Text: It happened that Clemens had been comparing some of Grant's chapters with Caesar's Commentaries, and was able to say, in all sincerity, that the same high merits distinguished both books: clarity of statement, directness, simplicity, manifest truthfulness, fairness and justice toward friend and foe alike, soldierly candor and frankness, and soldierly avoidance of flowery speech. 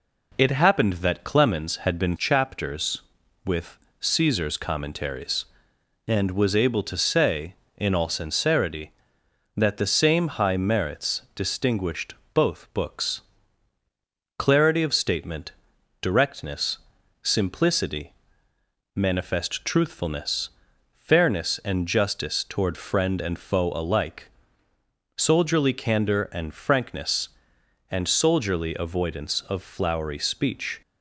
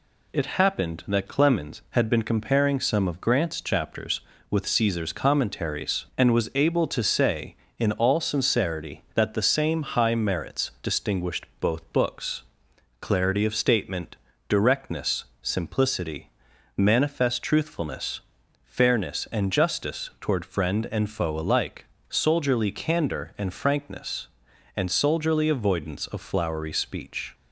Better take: second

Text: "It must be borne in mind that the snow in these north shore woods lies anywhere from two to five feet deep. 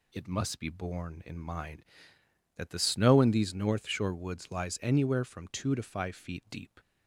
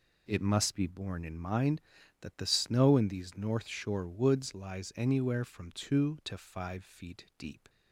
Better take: neither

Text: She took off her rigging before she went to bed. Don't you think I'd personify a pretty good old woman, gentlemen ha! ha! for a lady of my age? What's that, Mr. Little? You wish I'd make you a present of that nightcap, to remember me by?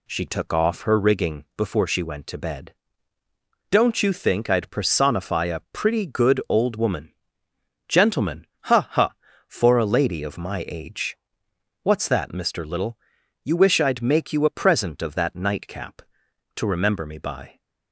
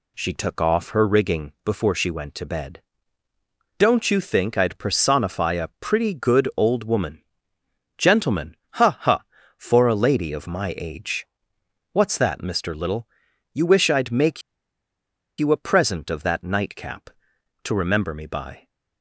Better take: first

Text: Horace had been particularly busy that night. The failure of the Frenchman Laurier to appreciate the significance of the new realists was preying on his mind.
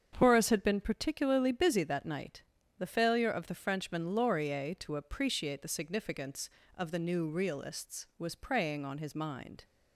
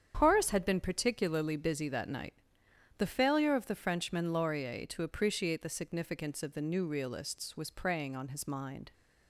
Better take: neither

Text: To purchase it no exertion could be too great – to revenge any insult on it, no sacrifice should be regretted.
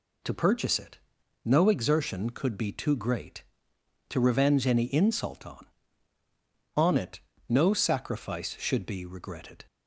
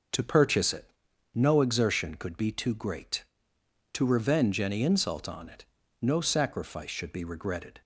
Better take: second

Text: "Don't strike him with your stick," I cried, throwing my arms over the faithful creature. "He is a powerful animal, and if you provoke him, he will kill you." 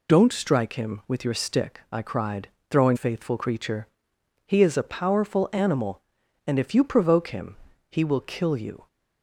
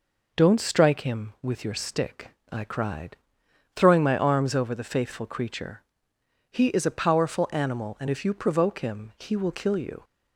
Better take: second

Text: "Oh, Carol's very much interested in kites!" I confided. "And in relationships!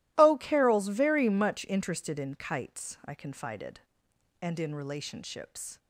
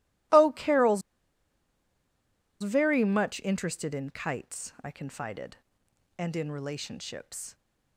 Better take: first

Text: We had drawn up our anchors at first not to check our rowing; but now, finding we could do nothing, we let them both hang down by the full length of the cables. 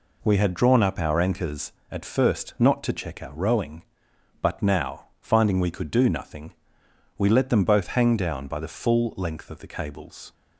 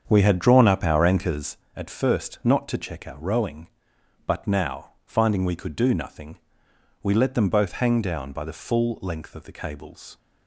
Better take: first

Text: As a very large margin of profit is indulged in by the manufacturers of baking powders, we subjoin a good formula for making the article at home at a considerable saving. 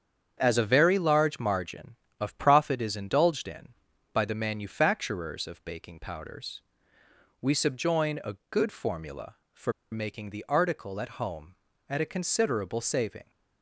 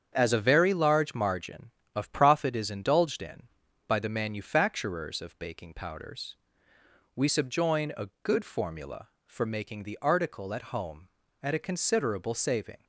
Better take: second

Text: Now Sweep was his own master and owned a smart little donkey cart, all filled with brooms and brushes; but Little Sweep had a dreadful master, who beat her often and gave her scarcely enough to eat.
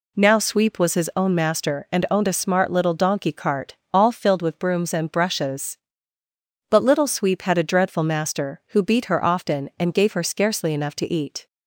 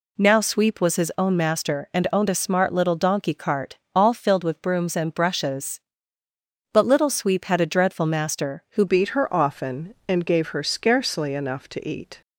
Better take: first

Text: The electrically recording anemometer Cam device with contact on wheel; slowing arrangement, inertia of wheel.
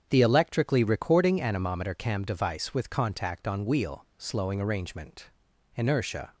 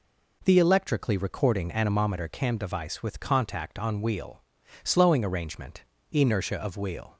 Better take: second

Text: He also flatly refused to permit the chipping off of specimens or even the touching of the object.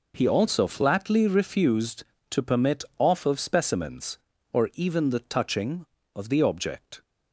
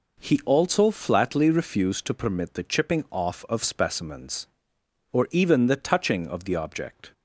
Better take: second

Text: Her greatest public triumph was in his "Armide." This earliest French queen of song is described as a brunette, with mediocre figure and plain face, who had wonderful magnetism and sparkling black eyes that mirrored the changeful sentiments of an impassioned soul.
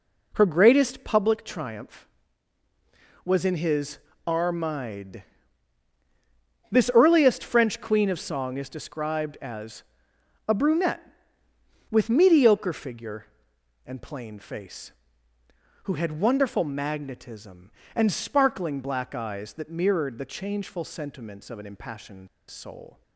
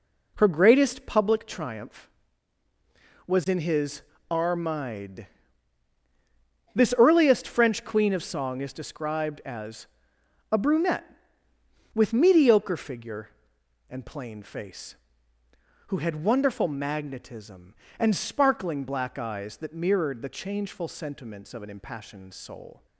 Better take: second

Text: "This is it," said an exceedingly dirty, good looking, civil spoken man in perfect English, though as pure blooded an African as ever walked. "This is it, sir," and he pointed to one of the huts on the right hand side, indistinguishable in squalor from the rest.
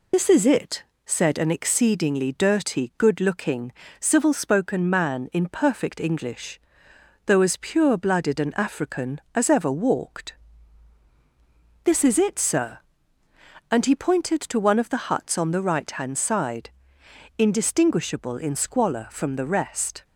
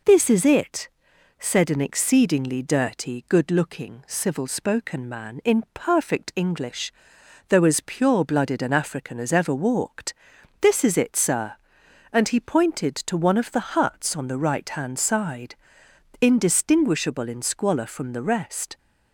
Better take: second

